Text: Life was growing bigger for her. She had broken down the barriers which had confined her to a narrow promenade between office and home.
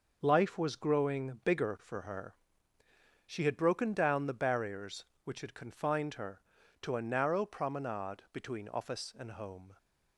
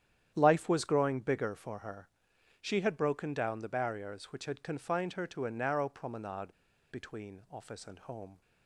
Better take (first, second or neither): first